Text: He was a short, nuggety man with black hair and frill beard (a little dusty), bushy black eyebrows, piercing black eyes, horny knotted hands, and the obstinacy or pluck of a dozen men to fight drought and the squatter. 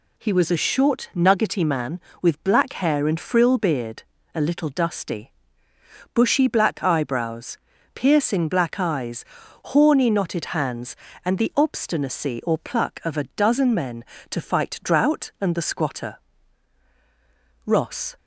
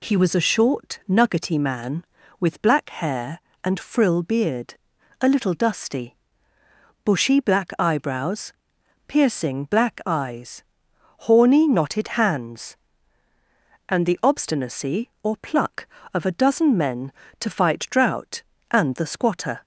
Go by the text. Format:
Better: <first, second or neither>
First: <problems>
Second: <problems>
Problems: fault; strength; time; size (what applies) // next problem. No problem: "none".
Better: second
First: goes on to say "Ross"; from 17.6 s on; 0.50 s long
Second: none